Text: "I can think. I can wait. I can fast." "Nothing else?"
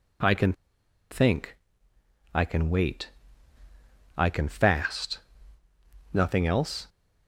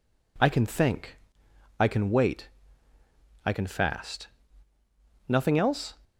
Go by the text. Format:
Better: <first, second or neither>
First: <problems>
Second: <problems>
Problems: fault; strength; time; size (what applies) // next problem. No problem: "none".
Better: second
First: pauses between "can" and "think"; noticeable; at 0.5 s; 0.57 s long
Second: none